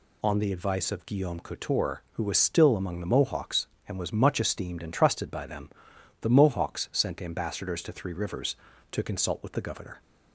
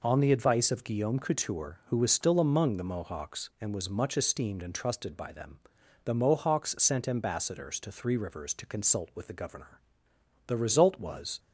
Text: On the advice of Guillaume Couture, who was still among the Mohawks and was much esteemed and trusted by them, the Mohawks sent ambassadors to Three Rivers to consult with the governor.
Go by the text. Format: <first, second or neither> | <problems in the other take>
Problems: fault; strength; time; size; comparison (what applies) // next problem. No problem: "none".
first | goes on to say "The result was"; noticeable; from 10.4 s on; 0.92 s long